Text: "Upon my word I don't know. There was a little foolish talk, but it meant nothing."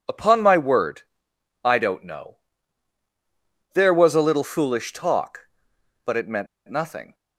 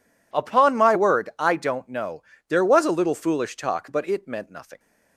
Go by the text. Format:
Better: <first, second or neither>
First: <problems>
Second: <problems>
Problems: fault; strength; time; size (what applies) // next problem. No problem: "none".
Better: second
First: pauses between "word" and "I"; noticeable; at 1.0 s; 0.60 s long // pauses between "meant" and "nothing"; slight; at 6.4 s; 0.21 s long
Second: none